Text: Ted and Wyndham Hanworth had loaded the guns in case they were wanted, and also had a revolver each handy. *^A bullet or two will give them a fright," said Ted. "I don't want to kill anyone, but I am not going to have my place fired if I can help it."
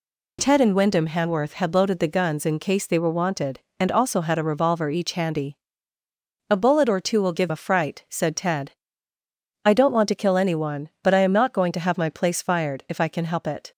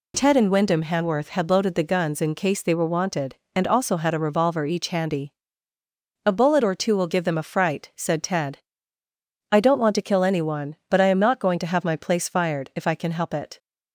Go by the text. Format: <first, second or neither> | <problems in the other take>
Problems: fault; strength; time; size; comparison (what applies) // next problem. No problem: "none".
second | skips "them"; at 7.4 s